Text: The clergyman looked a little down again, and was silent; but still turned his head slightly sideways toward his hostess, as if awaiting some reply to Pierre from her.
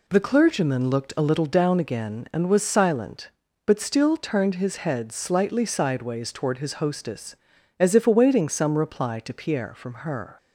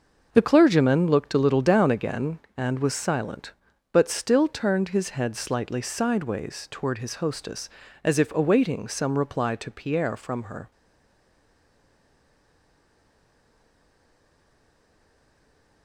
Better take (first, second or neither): first